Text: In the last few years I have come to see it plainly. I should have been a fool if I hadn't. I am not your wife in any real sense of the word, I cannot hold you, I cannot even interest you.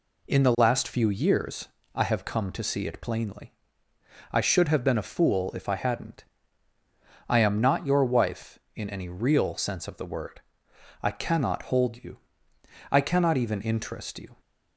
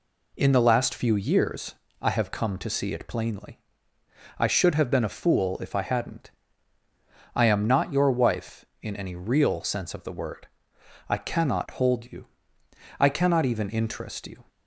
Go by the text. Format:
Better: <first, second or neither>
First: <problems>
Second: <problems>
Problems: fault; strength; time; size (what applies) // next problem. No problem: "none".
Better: neither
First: pauses between "years" and "I"; slight; at 1.6 s; 0.26 s long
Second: pauses between "years" and "I"; slight; at 1.7 s; 0.26 s long